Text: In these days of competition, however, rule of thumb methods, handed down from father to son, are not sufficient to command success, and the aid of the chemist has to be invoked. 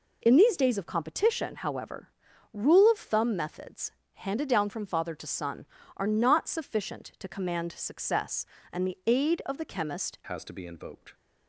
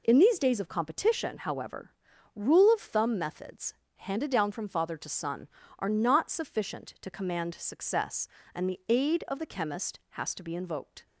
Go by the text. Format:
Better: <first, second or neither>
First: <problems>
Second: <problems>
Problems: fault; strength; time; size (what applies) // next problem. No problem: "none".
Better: second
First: changes voice at "has"; from 10.2 s on; 0.9 s long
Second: none